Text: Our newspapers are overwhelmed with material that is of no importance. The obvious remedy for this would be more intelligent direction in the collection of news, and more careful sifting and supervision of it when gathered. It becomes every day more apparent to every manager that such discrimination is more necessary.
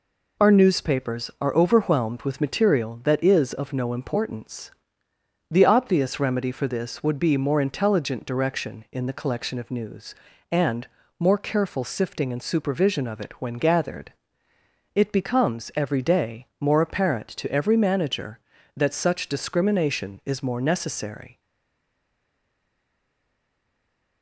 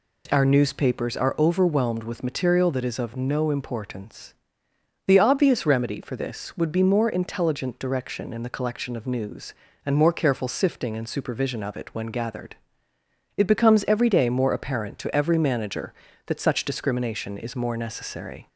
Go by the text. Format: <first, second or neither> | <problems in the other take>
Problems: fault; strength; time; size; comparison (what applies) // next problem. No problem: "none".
second | pauses between "and" and "more"; slight; at 10.8 s; 0.32 s long // stays silent after the last word; strong; from 21.3 s on; 2.9 s long